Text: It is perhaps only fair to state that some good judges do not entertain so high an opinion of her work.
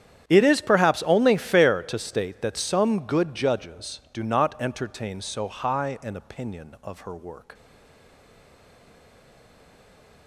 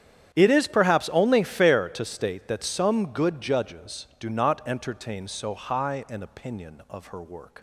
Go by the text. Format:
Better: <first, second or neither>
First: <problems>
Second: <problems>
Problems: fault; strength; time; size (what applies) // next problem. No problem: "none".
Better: second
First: starts louder than the rest; strong; until 1.2 s; 9.5 dB // stays silent after the last word; strong; from 7.5 s on; 2.7 s long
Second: starts louder than the rest; strong; until 1.3 s; 9.5 dB